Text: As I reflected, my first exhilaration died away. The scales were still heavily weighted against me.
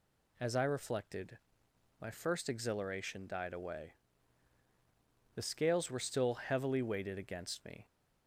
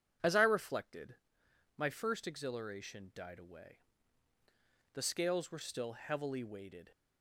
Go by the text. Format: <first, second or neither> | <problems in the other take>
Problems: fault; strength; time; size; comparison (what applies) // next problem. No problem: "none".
first | stops before "against me"; at 6.9 s